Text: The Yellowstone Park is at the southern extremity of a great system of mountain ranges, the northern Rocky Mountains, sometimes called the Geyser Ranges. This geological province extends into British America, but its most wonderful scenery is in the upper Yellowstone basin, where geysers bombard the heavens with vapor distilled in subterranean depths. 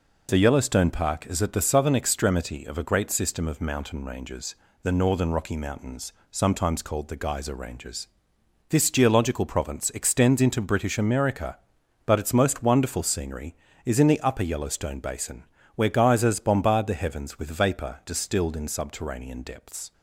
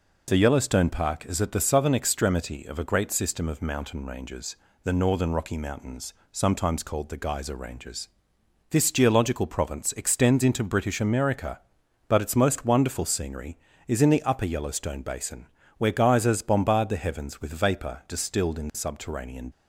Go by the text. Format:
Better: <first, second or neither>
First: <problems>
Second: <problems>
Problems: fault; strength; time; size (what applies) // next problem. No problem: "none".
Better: first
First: none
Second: stops before "depths"; at 19.5 s